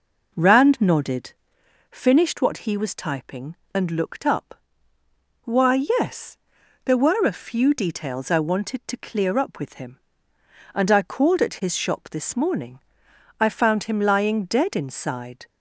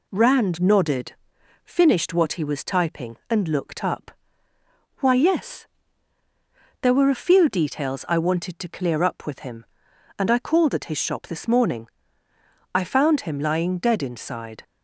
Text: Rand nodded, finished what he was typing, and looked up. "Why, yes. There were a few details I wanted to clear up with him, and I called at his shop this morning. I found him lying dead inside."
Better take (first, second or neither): second